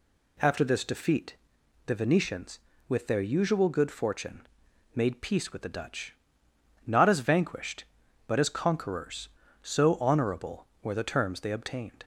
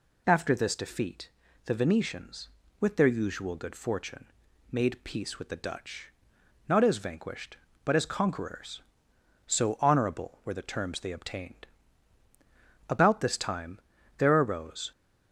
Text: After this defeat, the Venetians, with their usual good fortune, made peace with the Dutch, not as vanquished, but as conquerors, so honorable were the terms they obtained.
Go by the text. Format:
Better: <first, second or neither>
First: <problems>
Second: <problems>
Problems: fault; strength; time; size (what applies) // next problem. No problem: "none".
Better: first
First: none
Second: goes on to say "About this time there arose"; strong; from 12.8 s on; 2.0 s long